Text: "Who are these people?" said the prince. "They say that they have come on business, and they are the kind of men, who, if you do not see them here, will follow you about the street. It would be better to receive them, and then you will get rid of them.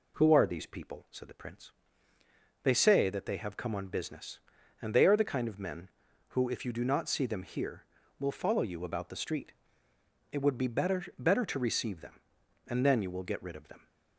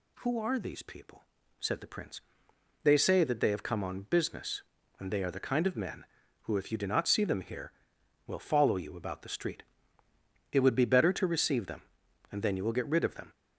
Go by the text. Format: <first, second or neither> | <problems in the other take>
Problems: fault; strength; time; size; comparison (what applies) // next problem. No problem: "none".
second | says "better" twice; at 11.1 s